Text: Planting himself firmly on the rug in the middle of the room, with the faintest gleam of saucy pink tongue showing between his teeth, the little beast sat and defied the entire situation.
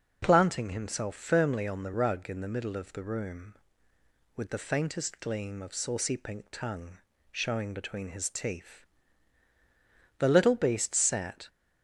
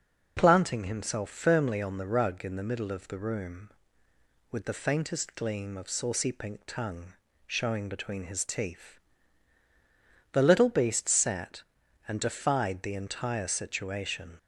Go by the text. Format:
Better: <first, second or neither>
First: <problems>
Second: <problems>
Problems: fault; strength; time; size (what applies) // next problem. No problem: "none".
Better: second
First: pauses between "tongue" and "showing"; slight; at 6.9 s; 0.34 s long // stops before "and defied the entire situation"; at 11.4 s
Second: pauses between "tongue" and "showing"; slight; at 7.1 s; 0.34 s long